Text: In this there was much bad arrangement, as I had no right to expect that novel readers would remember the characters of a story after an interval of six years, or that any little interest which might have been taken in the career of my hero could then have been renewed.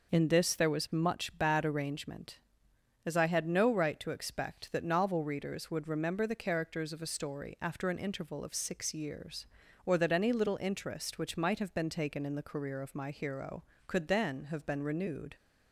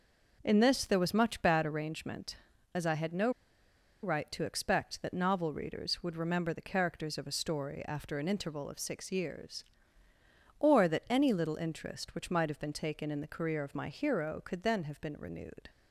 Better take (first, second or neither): first